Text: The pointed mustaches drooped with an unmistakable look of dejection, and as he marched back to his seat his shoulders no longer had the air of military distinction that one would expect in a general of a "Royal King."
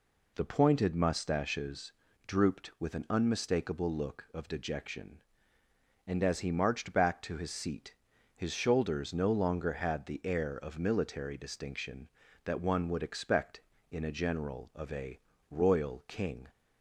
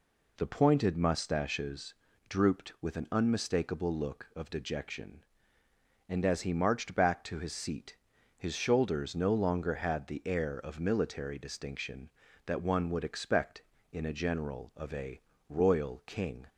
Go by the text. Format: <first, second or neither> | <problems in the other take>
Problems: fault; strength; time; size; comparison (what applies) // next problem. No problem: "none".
neither | pauses between "mustaches" and "drooped"; slight; the same in both // pauses between "seat" and "his"; the same in both // pauses between "a" and "Royal"; slight; the same in both